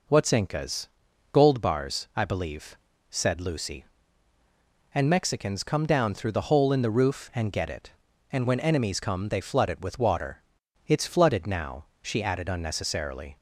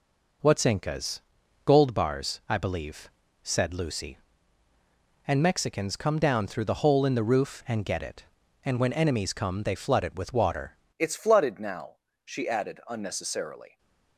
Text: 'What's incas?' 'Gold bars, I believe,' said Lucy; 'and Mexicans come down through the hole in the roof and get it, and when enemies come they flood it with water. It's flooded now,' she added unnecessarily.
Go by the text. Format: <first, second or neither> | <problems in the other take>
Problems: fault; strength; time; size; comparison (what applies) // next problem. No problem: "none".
first | changes voice at "It's"; from 10.9 s on; 2.8 s long